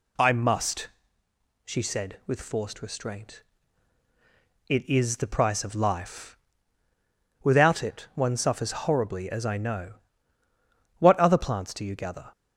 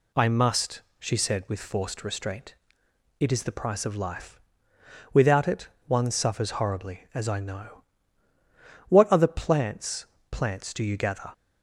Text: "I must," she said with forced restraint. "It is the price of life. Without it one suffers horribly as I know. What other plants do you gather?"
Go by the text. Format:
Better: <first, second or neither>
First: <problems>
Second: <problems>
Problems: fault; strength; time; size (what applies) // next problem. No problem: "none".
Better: first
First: none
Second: pauses between "it" and "one"; slight; at 5.6 s; 0.18 s long // says "plants" twice; at 10.2 s